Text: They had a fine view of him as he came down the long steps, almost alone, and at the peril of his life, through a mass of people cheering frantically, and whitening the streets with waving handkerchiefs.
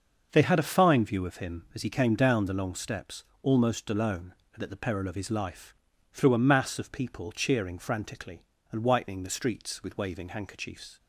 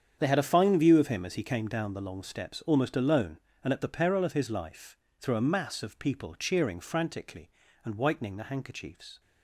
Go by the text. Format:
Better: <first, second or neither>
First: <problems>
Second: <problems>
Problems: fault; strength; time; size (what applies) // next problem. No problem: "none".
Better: first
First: starts louder than the rest; until 1.3 s; 6.5 dB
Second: starts louder than the rest; strong; until 1.2 s; 8 dB // skips "streets with waving"; at 8.4 s